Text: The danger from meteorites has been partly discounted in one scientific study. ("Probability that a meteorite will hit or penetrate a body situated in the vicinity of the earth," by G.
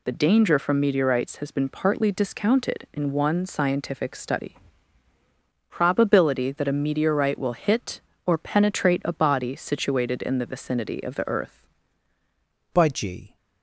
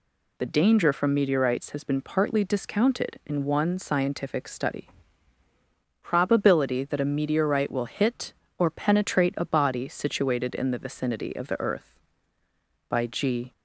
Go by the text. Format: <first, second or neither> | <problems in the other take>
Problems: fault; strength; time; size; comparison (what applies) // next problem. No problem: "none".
second | changes voice at "by"; from 12.7 s on; 0.6 s long